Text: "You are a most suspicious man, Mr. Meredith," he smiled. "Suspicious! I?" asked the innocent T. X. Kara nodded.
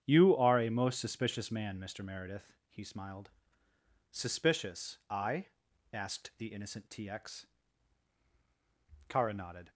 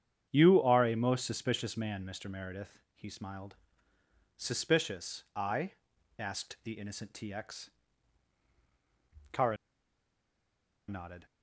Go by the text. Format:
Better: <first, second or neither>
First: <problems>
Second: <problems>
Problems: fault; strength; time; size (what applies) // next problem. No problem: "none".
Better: first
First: starts louder than the rest; strong; until 1.0 s; 8.5 dB // pauses between "X" and "Kara"; strong; at 7.4 s; 1.6 s long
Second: starts louder than the rest; strong; until 1.3 s; 8.5 dB // pauses between "X" and "Kara"; strong; at 7.6 s; 1.6 s long // pauses between "Kara" and "nodded"; strong; at 9.5 s; 1.3 s long